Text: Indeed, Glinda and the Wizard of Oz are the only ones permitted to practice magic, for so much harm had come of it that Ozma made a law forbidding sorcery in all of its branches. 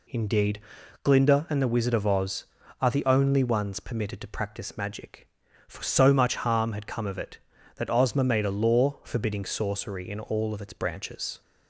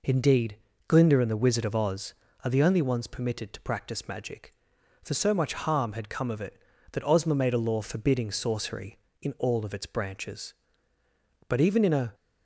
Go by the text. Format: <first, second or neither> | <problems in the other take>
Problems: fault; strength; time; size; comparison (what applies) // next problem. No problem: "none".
first | goes on to say "But even in a"; noticeable; from 11.4 s on; 0.66 s long